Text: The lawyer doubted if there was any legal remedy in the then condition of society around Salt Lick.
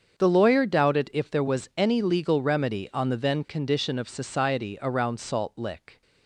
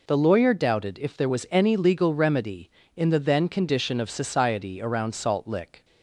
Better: second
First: starts louder than the rest; strong; until 1.2 s; 7 dB // says "on" for "in"; at 2.9 s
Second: none

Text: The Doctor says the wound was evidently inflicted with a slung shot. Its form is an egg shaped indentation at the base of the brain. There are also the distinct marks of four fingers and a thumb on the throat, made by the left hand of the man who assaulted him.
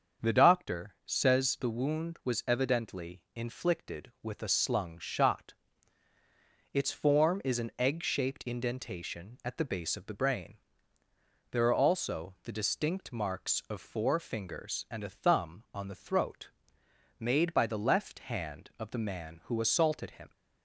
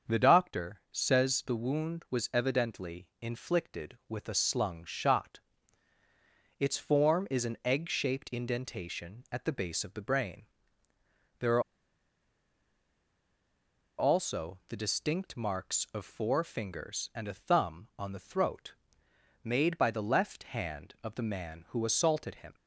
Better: first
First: starts louder than the rest; until 1.3 s; 7 dB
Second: starts louder than the rest; until 1.2 s; 7 dB // pauses between "are" and "also"; strong; at 11.6 s; 2.3 s long

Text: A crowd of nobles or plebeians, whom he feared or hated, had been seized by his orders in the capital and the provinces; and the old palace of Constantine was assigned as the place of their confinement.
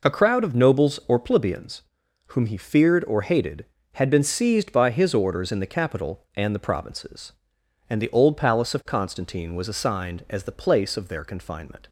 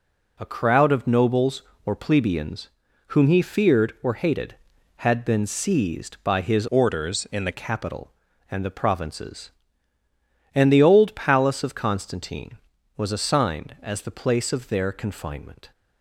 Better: first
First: none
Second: changes voice from "orders" to "the"; from 6.6 to 7.5 s; 0.9 s long

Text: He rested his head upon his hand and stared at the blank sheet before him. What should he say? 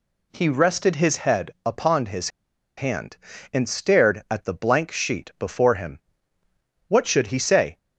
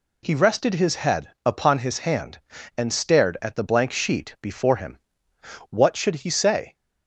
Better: second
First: pauses between "head" and "upon"; slight; at 1.5 s; 0.16 s long // pauses between "his" and "hand"; noticeable; at 2.2 s; 0.49 s long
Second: none

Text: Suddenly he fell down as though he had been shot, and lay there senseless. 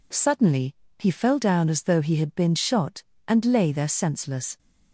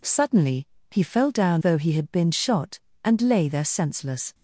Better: first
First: pauses between "Suddenly" and "he"; slight; at 0.7 s; 0.24 s long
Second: pauses between "Suddenly" and "he"; slight; at 0.6 s; 0.24 s long // skips "as"; at 1.6 s

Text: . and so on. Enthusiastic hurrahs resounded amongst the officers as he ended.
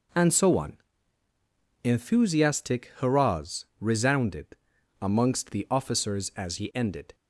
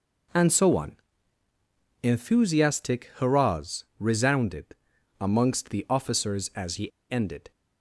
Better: first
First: pauses between "resounded" and "amongst"; at 4.5 s; 0.44 s long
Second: pauses between "resounded" and "amongst"; at 4.7 s; 0.44 s long // pauses between "he" and "ended"; slight; at 6.9 s; 0.20 s long

